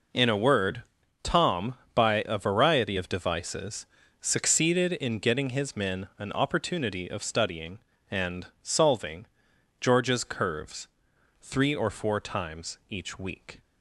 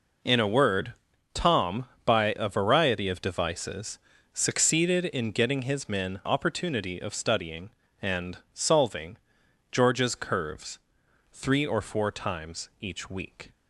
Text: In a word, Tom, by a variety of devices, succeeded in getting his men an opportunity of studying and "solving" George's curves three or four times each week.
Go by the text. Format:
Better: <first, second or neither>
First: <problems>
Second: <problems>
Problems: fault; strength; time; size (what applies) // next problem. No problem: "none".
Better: first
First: pauses between "and" and "solving"; slight; at 8.4 s; 0.16 s long // pauses between "solving" and "George's"; noticeable; at 9.2 s; 0.56 s long // pauses between "curves" and "three"; noticeable; at 10.8 s; 0.54 s long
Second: skips "an"; at 6.2 s // pauses between "and" and "solving"; slight; at 8.3 s; 0.16 s long // pauses between "solving" and "George's"; noticeable; at 9.1 s; 0.56 s long // pauses between "curves" and "three"; noticeable; at 10.7 s; 0.54 s long